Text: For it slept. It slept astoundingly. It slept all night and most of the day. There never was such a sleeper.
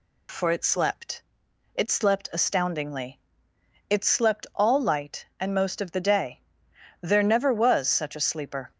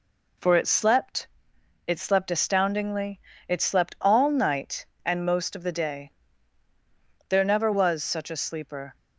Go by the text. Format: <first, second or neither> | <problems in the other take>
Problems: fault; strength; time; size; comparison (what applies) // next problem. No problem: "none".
second | says "light" for "night"; at 4.8 s